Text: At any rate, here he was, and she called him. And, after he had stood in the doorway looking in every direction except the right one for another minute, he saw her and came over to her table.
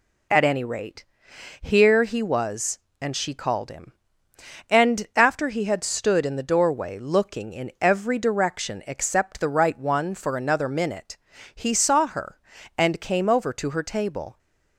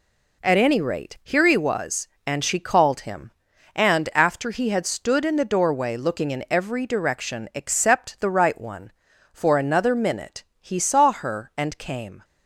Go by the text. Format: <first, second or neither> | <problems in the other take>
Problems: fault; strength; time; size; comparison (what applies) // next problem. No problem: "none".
first | stops before "over to her table"; at 12.2 s